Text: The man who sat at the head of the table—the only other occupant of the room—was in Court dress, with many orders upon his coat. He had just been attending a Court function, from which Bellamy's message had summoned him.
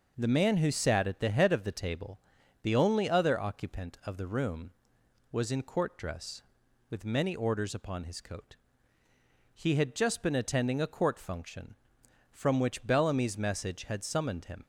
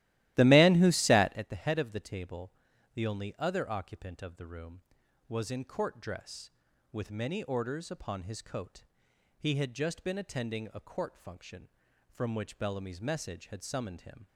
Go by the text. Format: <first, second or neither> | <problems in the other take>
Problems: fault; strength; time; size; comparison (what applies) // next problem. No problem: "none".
first | starts louder than the rest; strong; until 1.4 s; 15.5 dB